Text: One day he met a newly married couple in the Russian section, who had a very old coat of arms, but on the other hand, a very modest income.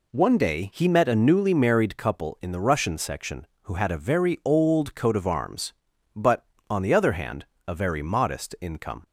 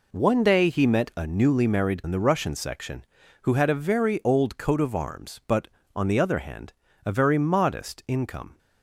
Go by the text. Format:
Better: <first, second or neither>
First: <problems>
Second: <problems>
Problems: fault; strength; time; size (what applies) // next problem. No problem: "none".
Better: first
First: none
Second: skips "couple"; at 2.0 s